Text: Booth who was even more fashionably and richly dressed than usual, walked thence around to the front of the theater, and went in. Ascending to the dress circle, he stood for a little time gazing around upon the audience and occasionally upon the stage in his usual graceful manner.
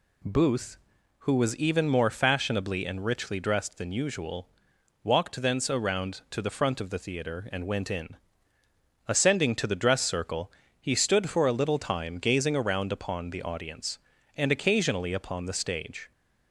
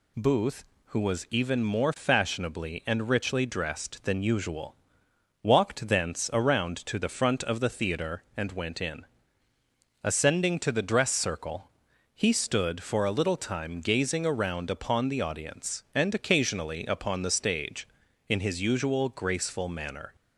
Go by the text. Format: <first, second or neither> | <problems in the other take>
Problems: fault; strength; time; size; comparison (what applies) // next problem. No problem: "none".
second | stops before "in his usual graceful manner"; at 16.1 s